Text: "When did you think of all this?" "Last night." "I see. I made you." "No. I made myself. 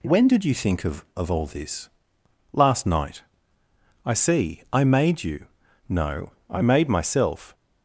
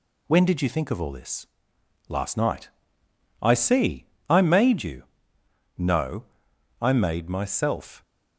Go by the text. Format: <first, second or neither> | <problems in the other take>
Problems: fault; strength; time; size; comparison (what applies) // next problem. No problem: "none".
second | says "of" twice; at 1.1 s